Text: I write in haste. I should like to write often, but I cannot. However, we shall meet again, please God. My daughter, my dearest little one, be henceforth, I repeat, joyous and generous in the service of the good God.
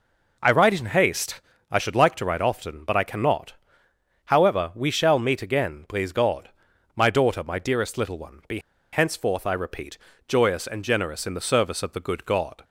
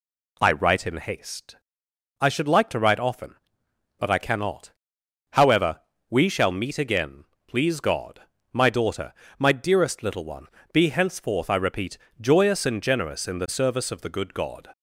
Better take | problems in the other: second | pauses between "be" and "henceforth"; slight; at 8.6 s; 0.32 s long

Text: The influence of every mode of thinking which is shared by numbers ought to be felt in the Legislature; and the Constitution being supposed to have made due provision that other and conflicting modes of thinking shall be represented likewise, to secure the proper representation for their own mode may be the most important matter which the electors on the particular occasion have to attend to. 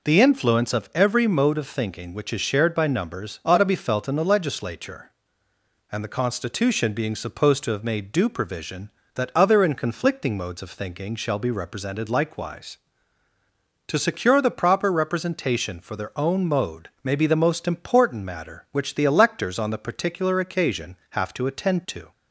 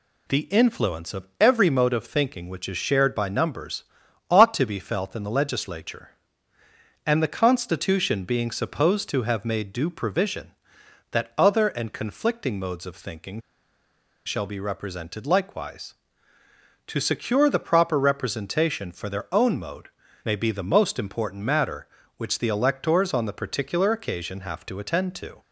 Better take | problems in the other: first | pauses between "numbers" and "ought"; at 3.8 s; 0.44 s long // pauses between "thinking" and "shall"; noticeable; at 13.3 s; 0.87 s long // pauses between "mode" and "may"; slight; at 19.8 s; 0.34 s long

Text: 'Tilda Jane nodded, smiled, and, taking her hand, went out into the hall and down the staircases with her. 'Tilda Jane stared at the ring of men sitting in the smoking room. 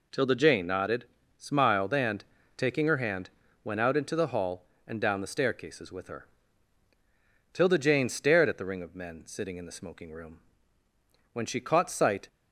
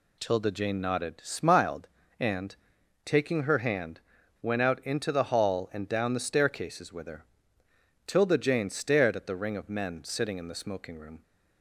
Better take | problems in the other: second | goes on to say "When she caught sight"; noticeable; from 11.3 s on; 0.94 s long

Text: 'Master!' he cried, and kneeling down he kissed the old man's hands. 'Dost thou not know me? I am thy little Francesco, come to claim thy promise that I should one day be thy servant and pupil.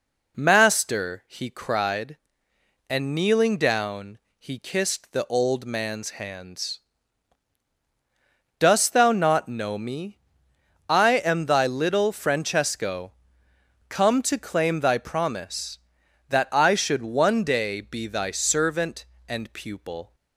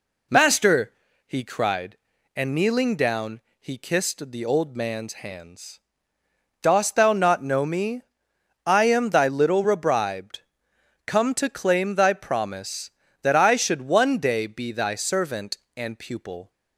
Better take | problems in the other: first | pauses between "down" and "he"; slight; at 3.4 s; 0.18 s long; slight in the first // says "Rebribed" for "Francesco"; at 9.6 s

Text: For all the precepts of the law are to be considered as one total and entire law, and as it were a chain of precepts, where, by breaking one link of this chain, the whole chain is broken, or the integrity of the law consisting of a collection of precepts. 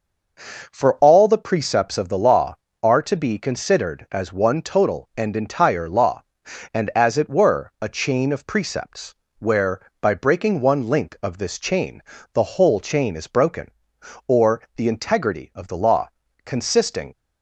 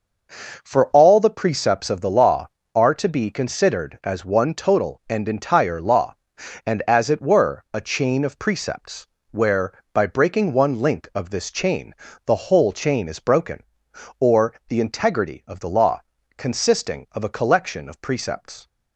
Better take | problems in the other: second | pauses between "law" and "consisting"; slight; at 16.0 s; 0.36 s long; slight in the second // stops before "of a collection of precepts"; at 17.1 s

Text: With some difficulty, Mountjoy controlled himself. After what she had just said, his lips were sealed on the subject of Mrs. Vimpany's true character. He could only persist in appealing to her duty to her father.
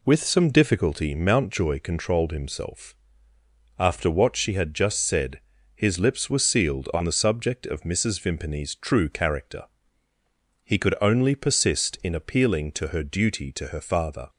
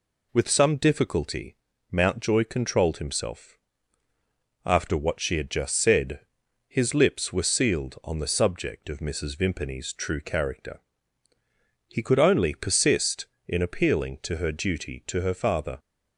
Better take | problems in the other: neither | none

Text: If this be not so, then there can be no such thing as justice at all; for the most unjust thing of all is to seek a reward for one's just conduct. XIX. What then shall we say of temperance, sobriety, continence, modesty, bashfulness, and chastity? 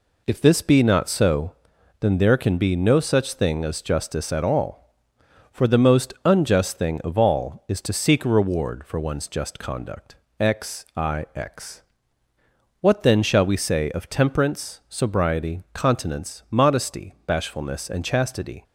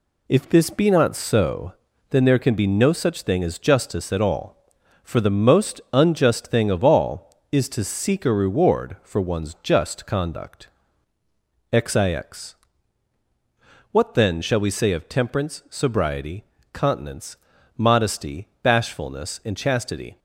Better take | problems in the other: neither | none

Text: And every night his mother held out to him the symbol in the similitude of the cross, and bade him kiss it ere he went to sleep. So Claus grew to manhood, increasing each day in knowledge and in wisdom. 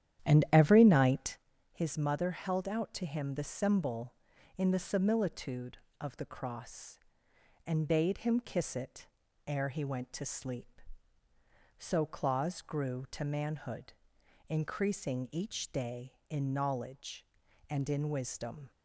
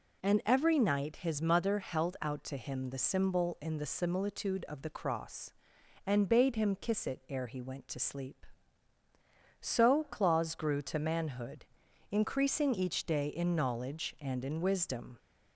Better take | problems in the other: second | starts louder than the rest; strong; until 1.5 s; 10.5 dB // pauses between "night" and "his"; slight; at 1.3 s; 0.36 s long // pauses between "it" and "ere"; at 9.0 s; 0.40 s long

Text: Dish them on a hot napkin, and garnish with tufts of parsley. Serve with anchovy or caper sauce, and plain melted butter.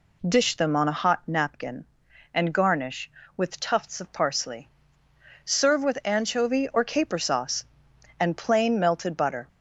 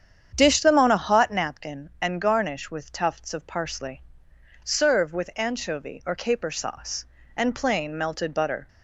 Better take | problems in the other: first | starts louder than the rest; strong; until 1.7 s; 8.5 dB

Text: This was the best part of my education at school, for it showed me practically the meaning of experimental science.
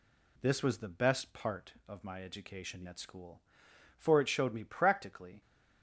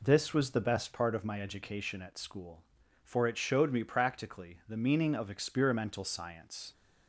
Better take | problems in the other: second | stops before "the meaning of experimental science"; at 5.4 s

